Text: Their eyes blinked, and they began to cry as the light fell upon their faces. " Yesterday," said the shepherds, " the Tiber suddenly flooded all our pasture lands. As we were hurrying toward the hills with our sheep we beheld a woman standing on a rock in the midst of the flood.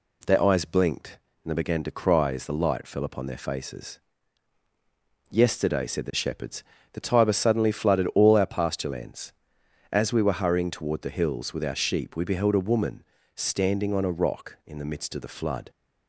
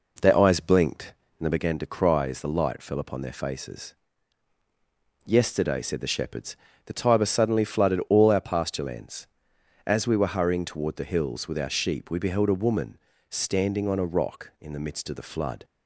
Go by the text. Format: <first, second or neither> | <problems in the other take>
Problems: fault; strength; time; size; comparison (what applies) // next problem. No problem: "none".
first | starts louder than the rest; noticeable; until 1.7 s; 4.5 dB // pauses between "woman" and "standing"; slight; at 12.9 s; 0.32 s long; slight in the first